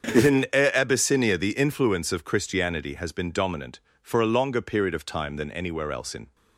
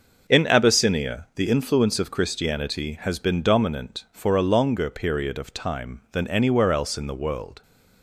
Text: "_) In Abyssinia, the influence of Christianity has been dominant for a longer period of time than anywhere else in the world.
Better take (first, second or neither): second